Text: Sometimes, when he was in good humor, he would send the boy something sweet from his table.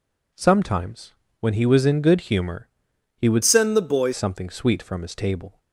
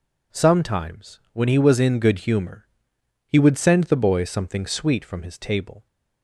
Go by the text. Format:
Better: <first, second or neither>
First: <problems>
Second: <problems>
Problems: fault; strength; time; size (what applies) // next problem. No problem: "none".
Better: second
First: changes voice from "send" to "boy"; from 3.4 to 4.1 s; 0.7 s long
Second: none